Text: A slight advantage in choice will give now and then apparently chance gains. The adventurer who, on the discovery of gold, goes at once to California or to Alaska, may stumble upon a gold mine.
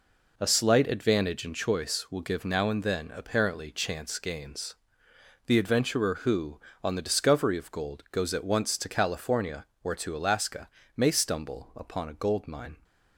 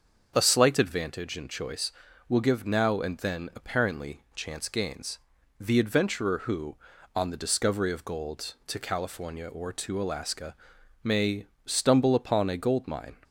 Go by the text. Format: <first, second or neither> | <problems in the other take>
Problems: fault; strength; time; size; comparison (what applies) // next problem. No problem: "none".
first | starts louder than the rest; until 1.3 s; 6.5 dB // skips "goes at once"; at 8.6 s // pauses between "may" and "stumble"; slight; at 11.4 s; 0.20 s long